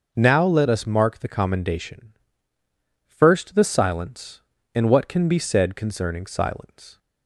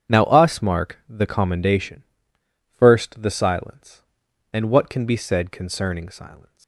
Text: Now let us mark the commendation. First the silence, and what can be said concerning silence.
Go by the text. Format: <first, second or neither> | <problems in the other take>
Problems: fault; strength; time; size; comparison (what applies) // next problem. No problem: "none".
first | starts louder than the rest; strong; until 1.1 s; 8.5 dB; noticeable in the first // skips "let"; at 0.2 s